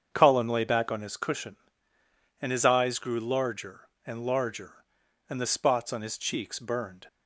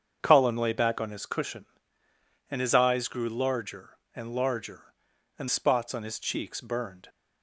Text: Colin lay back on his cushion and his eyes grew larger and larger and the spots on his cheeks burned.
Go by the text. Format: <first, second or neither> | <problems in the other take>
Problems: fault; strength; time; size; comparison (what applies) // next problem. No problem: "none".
first | starts louder than the rest; strong; until 1.2 s; 7 dB; strong in the first // skips "the"; at 5.4 s